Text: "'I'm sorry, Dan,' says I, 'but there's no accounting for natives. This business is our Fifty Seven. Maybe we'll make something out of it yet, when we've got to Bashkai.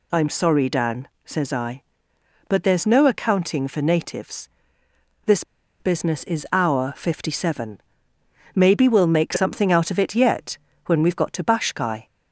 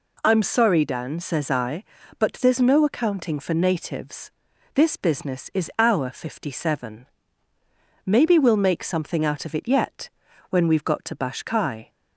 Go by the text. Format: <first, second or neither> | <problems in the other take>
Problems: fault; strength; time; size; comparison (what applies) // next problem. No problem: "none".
second | pauses between "This" and "business"; at 5.4 s; 0.37 s long